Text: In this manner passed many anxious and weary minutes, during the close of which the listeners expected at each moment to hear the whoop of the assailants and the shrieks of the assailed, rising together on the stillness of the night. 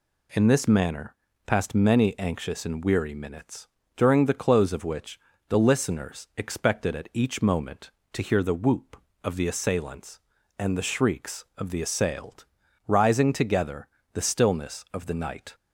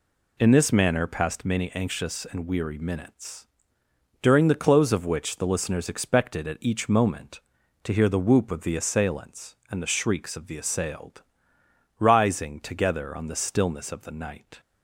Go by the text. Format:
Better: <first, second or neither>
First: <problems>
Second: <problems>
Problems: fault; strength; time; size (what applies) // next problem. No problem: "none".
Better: second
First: pauses between "manner" and "passed"; slight; at 1.1 s; 0.30 s long // pauses between "which" and "the"; slight; at 5.1 s; 0.30 s long // skips "on"; at 13.9 s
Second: none